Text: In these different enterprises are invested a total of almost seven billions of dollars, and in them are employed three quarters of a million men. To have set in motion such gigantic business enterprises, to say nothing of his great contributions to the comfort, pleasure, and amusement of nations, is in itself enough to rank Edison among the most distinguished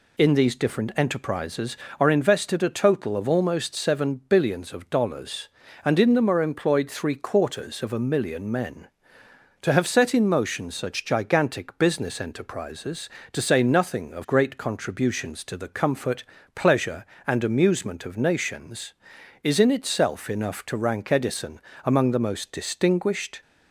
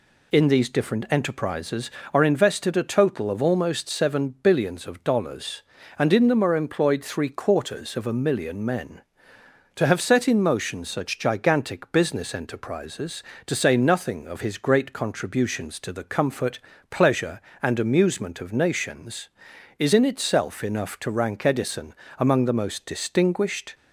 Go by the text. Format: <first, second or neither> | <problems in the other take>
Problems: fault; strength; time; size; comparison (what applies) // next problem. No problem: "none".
second | skips "his"; at 14.2 s // pauses between "Edison" and "among"; slight; at 21.5 s; 0.24 s long; slight in the second